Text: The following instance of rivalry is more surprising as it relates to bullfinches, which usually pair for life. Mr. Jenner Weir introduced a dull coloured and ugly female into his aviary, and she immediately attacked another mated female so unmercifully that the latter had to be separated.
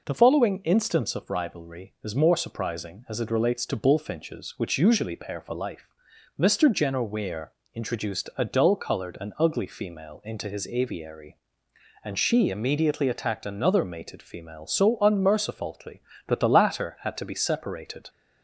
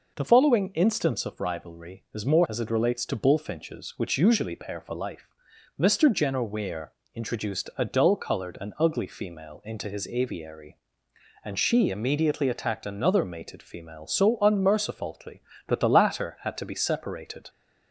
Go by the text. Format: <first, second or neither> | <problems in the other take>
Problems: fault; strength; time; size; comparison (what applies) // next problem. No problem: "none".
first | skips "surprising"; at 2.4 s // pauses between "Weir" and "introduced"; slight; at 6.9 s; 0.24 s long; slight in the first